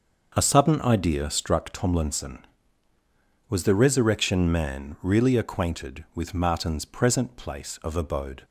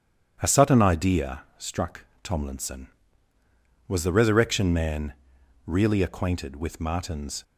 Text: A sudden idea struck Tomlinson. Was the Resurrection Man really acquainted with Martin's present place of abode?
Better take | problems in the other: first | starts louder than the rest; strong; until 1.4 s; 9 dB; also in the first // pauses between "idea" and "struck"; slight; at 1.4 s; 0.16 s long // pauses between "struck" and "Tomlinson"; slight; at 2.0 s; 0.18 s long // pauses between "Man" and "really"; noticeable; at 5.1 s; 0.54 s long // stops before "present place of abode"; at 7.4 s

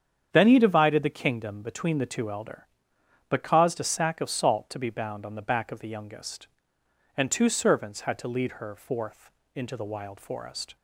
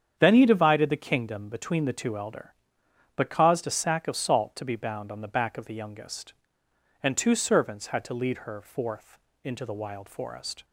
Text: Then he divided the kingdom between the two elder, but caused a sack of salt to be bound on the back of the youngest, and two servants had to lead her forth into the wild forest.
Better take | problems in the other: neither | starts louder than the rest; strong; the same in both // pauses between "forth" and "into"; slight; the same in both

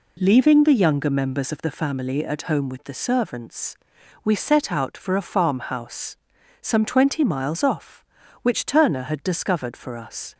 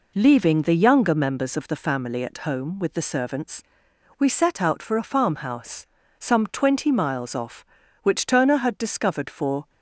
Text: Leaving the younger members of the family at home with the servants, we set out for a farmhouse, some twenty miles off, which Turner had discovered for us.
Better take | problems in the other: first | stops before "us"; at 9.6 s

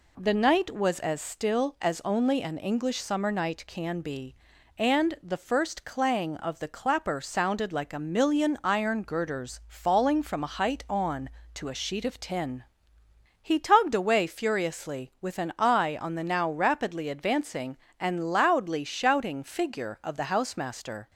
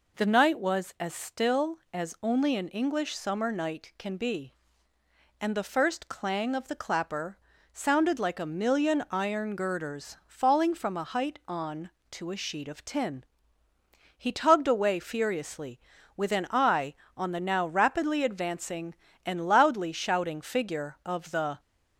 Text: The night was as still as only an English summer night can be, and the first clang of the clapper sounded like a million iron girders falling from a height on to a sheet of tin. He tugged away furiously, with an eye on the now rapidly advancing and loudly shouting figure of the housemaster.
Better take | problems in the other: first | pauses between "clapper" and "sounded"; slight; at 7.3 s; 0.36 s long // stops before "housemaster"; at 21.5 s

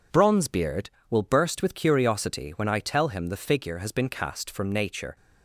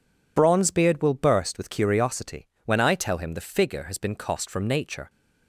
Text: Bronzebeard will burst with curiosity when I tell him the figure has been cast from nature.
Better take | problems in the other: first | pauses between "curiosity" and "when"; slight; at 2.4 s; 0.20 s long // says "cost" for "cast"; at 4.1 s

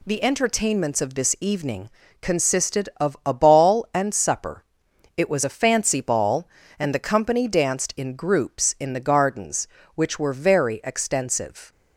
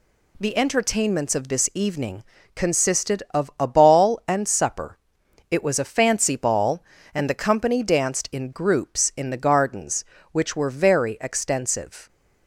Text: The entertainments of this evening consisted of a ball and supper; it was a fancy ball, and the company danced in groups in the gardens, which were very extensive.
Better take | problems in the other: neither | pauses between "evening" and "consisted"; slight; the same in both

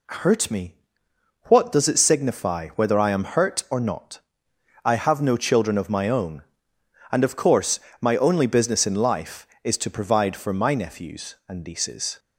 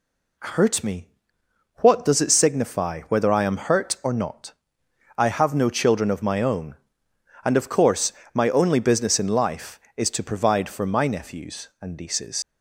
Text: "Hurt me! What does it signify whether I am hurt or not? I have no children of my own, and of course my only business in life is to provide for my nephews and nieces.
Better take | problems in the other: first | pauses between "course" and "my"; slight; at 8.1 s; 0.22 s long; slight in the first // leaves "nieces" unfinished; at 12.4 s; 95 ms

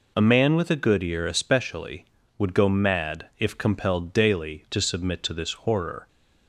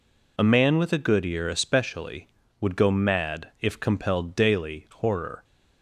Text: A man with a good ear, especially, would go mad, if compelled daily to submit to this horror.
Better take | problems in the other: first | skips "to submit to this"; at 4.8 s

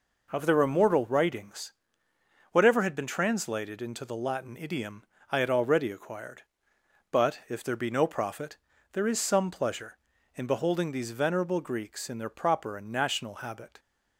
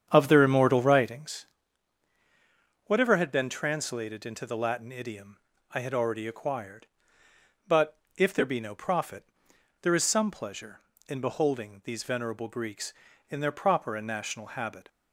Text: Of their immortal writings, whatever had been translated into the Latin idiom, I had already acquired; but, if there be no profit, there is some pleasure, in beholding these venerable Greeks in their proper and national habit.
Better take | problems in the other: first | starts louder than the rest; strong; until 1.3 s; 8 dB

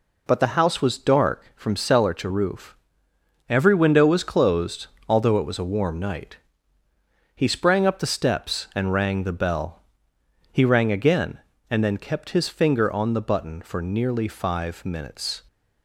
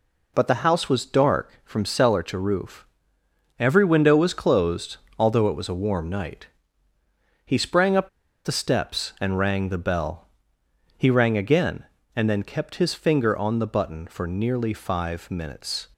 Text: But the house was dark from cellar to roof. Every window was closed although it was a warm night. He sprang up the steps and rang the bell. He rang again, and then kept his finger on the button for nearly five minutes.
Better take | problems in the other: first | pauses between "closed" and "although"; slight; at 4.9 s; 0.20 s long; slight in the first // pauses between "up" and "the"; slight; at 8.0 s; 0.36 s long

